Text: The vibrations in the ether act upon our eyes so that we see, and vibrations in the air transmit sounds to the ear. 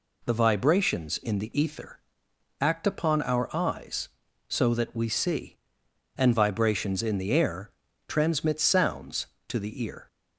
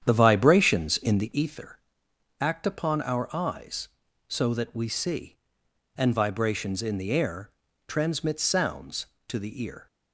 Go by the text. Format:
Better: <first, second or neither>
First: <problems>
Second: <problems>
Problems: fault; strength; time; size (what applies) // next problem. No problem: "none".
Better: first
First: pauses between "ether" and "act"; noticeable; at 1.9 s; 0.62 s long // pauses between "air" and "transmit"; slight; at 7.7 s; 0.36 s long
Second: starts louder than the rest; strong; until 1.4 s; 9 dB // pauses between "ether" and "act"; noticeable; at 1.7 s; 0.62 s long // pauses between "air" and "transmit"; slight; at 7.5 s; 0.36 s long